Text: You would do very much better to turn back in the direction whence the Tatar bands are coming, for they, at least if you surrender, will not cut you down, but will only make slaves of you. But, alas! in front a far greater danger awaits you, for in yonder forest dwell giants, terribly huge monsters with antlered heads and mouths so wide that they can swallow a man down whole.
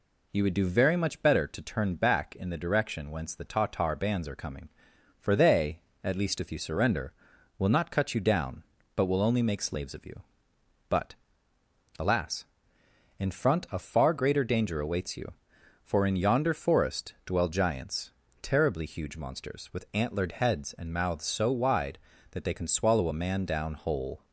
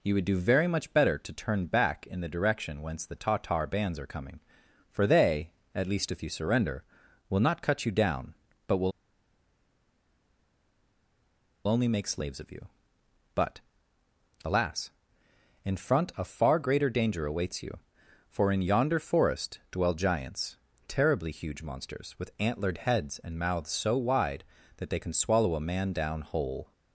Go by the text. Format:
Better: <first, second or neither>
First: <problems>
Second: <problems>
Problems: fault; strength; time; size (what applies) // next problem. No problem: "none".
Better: first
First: none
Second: pauses between "will" and "only"; strong; at 8.9 s; 2.7 s long